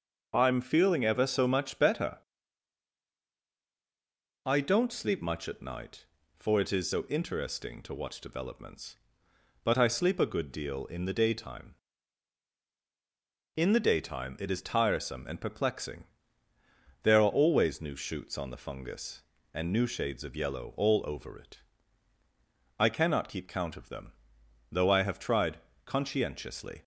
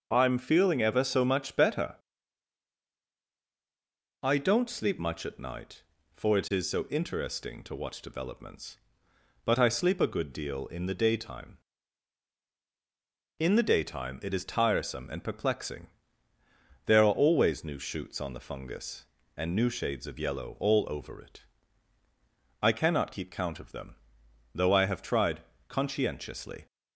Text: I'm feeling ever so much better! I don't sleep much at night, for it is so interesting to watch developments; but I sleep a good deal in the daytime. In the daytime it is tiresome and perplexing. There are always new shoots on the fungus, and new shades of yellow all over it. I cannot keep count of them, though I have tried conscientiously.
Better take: neither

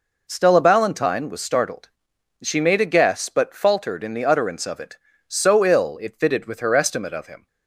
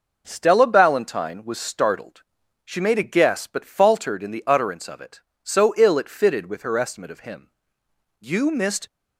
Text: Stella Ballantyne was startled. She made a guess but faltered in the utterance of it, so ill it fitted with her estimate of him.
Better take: first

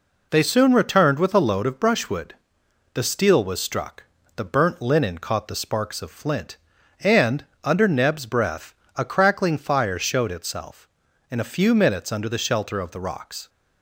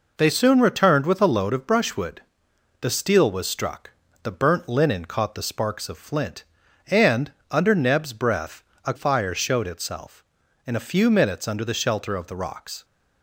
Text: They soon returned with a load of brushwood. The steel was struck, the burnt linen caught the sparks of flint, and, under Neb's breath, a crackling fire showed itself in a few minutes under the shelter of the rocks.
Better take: first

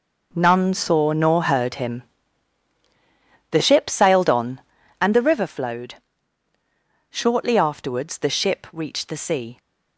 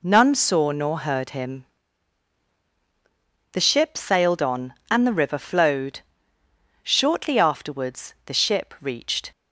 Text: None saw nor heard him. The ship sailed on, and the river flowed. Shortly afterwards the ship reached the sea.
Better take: first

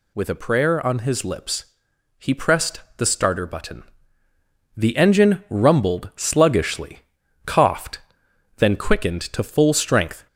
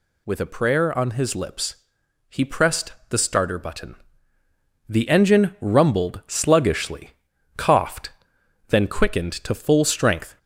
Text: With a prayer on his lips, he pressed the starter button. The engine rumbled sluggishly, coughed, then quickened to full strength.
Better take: neither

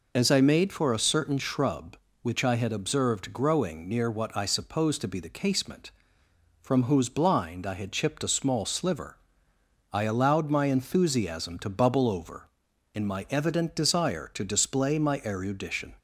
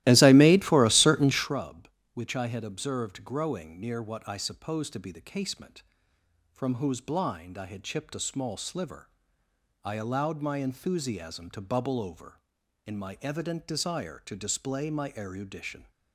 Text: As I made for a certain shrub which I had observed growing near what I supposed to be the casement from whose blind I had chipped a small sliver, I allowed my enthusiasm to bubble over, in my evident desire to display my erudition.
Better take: first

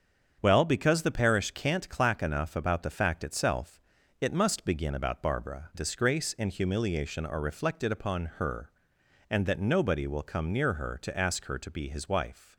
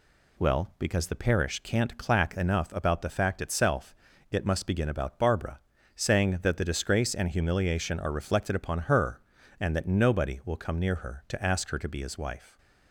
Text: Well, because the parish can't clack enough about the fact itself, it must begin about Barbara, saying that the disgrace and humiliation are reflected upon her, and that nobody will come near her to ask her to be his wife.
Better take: second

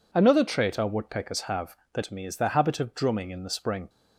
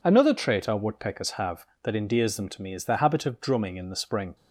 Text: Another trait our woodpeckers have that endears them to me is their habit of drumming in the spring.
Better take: second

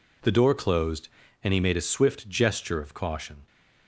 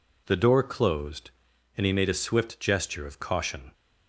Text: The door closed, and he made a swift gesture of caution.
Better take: neither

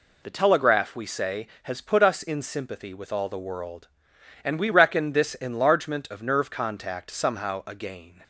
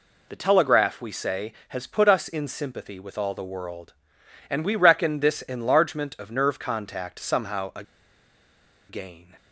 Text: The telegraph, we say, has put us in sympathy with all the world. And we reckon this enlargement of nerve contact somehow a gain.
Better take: first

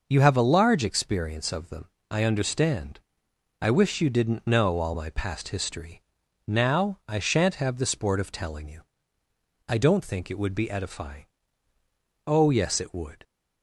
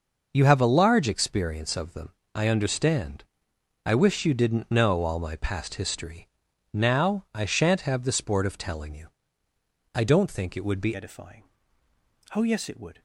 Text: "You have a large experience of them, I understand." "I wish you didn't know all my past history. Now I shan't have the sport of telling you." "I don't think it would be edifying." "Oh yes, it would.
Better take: first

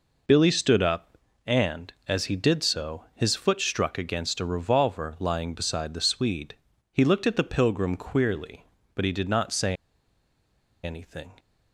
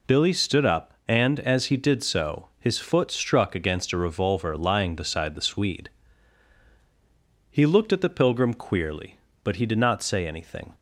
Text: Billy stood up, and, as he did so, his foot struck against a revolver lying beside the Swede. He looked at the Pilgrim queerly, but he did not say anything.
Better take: second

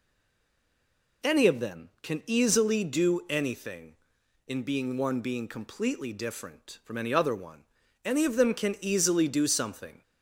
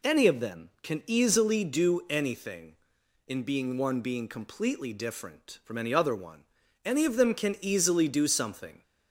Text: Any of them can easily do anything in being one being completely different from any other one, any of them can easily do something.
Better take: second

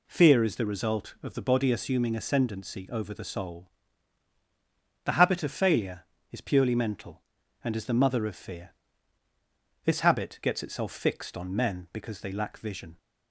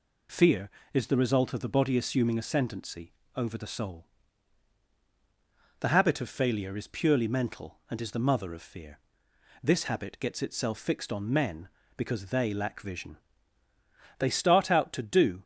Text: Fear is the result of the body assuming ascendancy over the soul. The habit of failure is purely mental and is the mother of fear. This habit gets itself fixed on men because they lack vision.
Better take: first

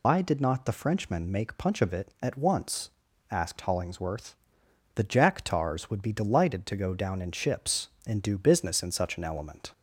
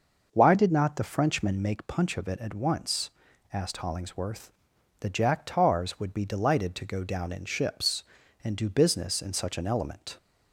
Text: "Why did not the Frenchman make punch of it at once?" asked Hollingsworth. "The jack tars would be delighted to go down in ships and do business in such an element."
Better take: second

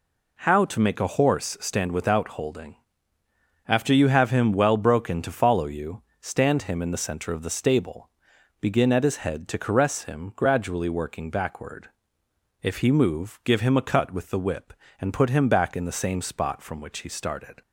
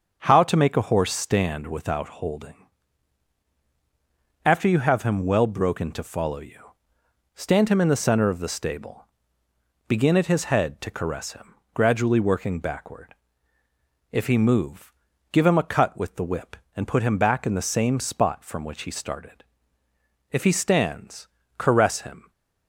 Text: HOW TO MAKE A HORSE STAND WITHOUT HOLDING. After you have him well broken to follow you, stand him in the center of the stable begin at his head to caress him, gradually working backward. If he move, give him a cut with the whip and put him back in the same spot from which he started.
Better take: first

